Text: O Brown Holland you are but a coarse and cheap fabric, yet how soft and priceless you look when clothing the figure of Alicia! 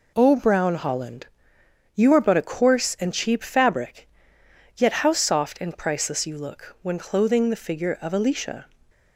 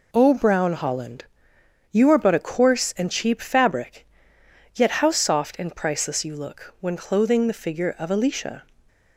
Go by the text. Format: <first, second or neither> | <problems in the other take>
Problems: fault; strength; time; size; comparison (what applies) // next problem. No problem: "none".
neither | pauses between "Holland" and "you"; noticeable; the same in both